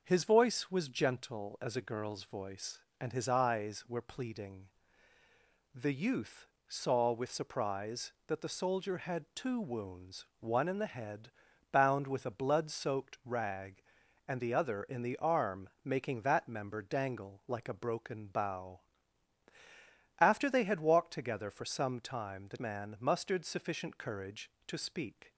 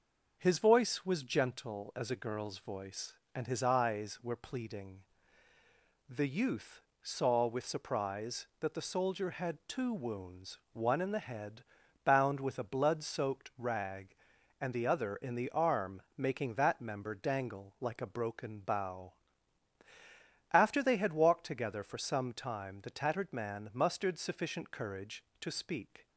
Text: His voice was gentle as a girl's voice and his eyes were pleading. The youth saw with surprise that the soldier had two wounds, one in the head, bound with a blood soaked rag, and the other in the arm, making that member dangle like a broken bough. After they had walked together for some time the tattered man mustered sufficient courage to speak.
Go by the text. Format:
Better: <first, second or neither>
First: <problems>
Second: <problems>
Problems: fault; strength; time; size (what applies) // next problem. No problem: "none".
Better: second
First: pauses between "youth" and "saw"; slight; at 6.4 s; 0.22 s long // skips "tattered"; at 22.5 s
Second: pauses between "youth" and "saw"; slight; at 6.7 s; 0.22 s long